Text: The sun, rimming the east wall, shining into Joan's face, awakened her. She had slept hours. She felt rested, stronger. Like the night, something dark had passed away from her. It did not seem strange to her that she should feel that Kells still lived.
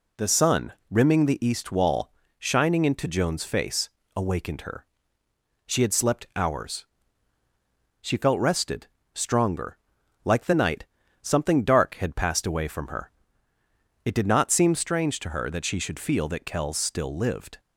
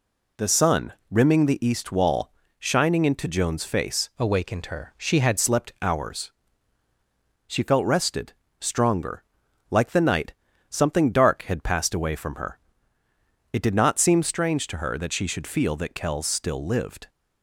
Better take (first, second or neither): first